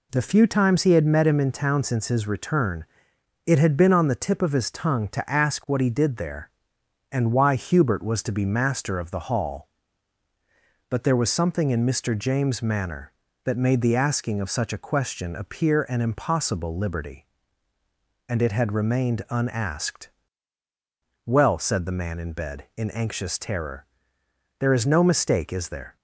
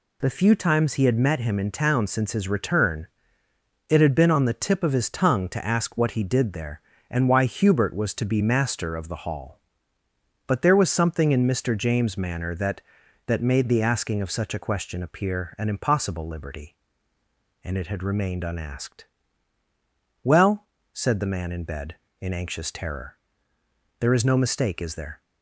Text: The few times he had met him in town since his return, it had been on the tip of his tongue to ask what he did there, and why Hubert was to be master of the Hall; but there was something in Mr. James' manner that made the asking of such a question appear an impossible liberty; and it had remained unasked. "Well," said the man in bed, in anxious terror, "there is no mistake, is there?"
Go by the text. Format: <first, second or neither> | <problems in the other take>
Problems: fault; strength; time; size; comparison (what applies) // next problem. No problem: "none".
first | says "that" twice; at 13.2 s